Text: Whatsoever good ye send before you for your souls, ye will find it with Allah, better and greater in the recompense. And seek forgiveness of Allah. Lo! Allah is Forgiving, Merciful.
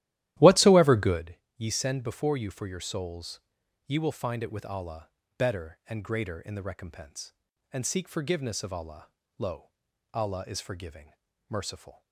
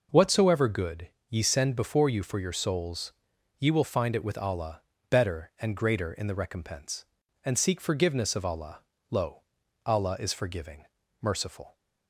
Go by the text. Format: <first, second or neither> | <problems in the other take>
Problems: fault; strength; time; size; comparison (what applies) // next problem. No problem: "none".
second | starts louder than the rest; strong; until 1.3 s; 14 dB // pauses between "good" and "ye"; slight; at 1.3 s; 0.20 s long; slight in the second